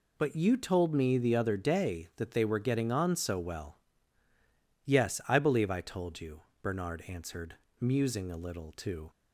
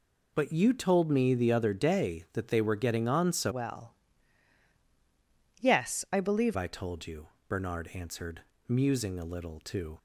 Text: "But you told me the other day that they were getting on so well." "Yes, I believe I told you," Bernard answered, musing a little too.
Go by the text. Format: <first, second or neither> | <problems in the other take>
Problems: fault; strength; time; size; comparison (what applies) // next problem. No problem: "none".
first | changes voice from "well" to "believe"; from 3.4 to 6.5 s; 3.1 s long